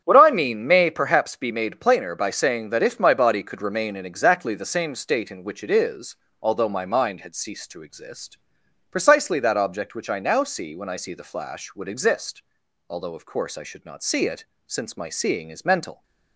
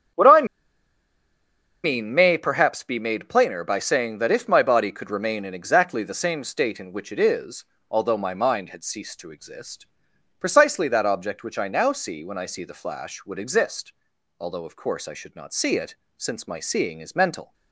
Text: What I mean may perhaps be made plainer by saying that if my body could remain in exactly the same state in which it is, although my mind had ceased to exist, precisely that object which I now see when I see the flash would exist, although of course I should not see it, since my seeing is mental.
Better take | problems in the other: first | starts louder than the rest; strong; until 2.5 s; 8.5 dB; strong in the first // pauses between "I" and "mean"; strong; at 0.4 s; 1.3 s long

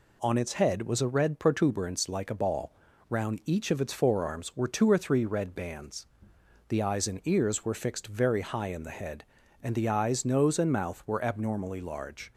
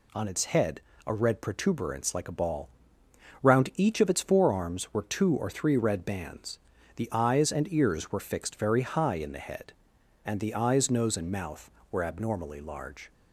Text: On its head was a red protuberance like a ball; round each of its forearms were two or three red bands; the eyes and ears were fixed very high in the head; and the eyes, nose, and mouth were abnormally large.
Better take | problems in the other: first | skips "was"; at 0.9 s

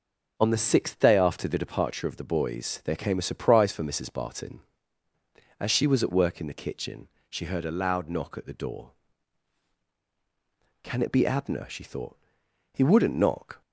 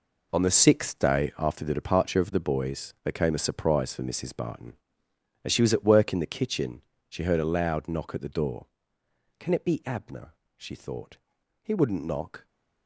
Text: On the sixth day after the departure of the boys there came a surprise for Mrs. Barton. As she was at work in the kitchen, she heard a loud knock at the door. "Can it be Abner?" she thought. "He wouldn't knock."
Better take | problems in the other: first | gets quieter; strong; throughout; 11.5 dB

